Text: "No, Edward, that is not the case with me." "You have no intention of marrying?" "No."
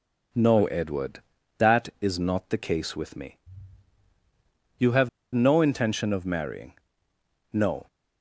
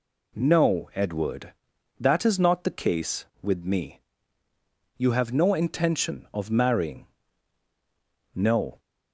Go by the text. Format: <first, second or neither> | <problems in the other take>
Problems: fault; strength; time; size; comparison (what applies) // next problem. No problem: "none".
second | pauses between "have" and "no"; slight; at 5.0 s; 0.25 s long